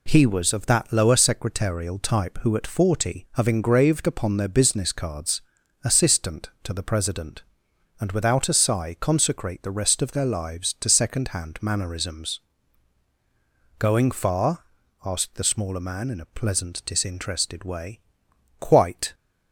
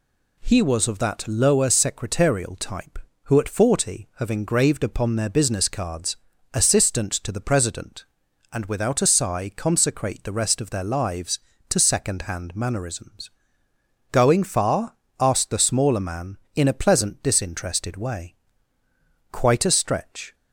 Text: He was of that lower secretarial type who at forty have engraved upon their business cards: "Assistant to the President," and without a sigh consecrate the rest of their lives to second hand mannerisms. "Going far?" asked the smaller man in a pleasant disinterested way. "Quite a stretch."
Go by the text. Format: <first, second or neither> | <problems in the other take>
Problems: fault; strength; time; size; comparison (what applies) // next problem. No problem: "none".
second | stops before "a stretch"; at 19.1 s